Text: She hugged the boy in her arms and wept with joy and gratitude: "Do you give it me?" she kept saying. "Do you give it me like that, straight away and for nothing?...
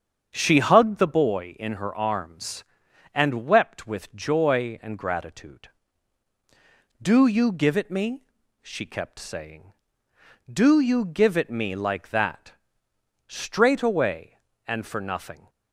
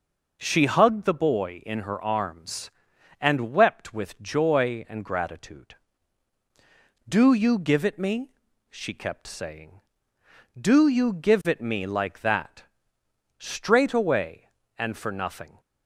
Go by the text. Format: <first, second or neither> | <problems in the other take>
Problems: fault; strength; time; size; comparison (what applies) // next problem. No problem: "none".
second | starts louder than the rest; strong; until 1.3 s; 7.5 dB